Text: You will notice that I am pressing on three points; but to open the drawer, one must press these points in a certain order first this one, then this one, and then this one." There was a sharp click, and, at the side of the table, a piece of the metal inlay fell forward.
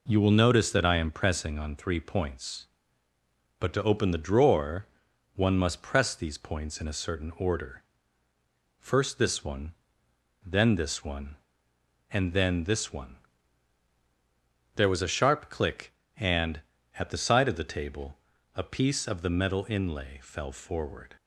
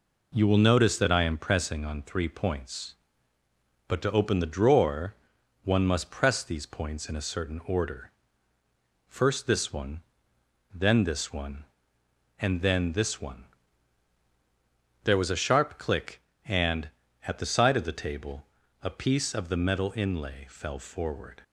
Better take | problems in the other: neither | pauses between "order" and "first"; noticeable; the same in both

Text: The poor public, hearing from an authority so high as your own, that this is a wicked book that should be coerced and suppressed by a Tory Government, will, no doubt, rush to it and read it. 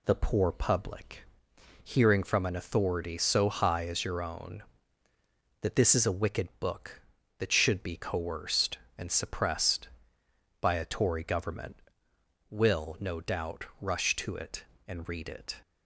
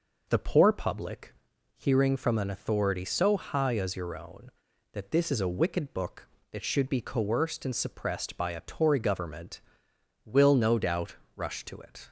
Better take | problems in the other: first | stops before "and read it"; at 12.0 s

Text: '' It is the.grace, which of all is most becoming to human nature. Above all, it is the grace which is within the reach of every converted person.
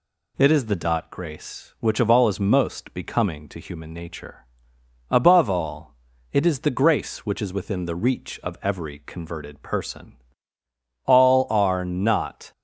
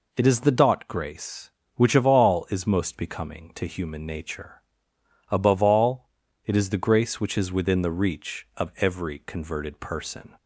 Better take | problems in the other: second | goes on to say "All are not"; from 11.0 s on; 1.4 s long

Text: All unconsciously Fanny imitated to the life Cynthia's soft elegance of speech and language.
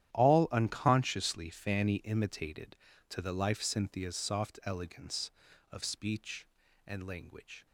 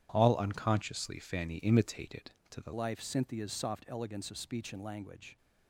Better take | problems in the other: first | starts louder than the rest; strong; until 1.1 s; 10.5 dB; strong in the first // changes voice at "life"; from 2.7 s on; 2.6 s long

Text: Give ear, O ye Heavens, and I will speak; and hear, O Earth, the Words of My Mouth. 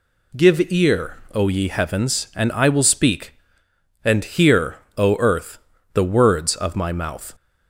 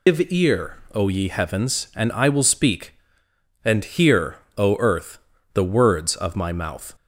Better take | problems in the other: first | loses the start of "Give"; at 0.0 s; 125 ms

